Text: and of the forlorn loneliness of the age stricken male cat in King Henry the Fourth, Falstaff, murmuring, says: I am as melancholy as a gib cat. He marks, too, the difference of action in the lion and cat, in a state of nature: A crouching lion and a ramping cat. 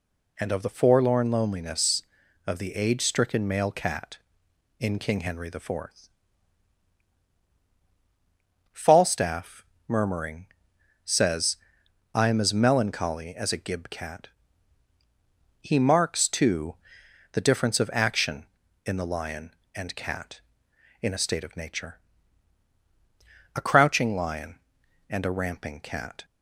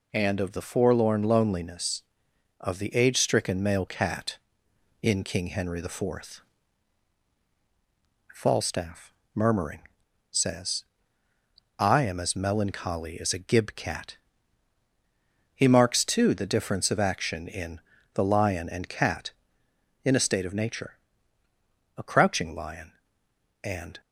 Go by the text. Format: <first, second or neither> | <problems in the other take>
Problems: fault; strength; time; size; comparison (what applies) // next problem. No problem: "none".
first | pauses between "in" and "the"; slight; at 17.8 s; 0.34 s long // stops before "a ramping cat"; at 24.0 s